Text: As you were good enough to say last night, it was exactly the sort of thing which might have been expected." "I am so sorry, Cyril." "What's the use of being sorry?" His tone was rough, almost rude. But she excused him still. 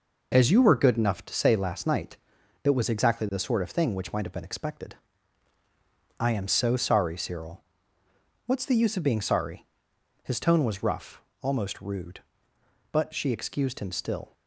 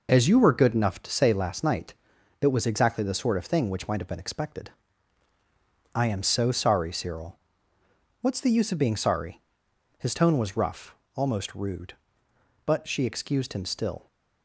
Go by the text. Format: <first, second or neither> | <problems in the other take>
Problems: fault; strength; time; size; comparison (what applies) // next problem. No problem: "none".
neither | none